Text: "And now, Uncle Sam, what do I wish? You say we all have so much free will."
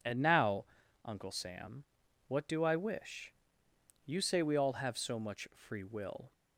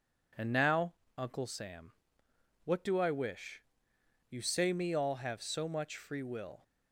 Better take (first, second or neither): first